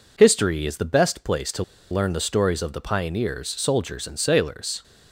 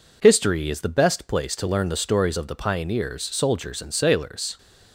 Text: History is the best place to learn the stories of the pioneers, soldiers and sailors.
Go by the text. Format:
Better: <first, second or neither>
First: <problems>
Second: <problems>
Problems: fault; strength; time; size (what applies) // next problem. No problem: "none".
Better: second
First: pauses between "to" and "learn"; slight; at 1.6 s; 0.28 s long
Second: none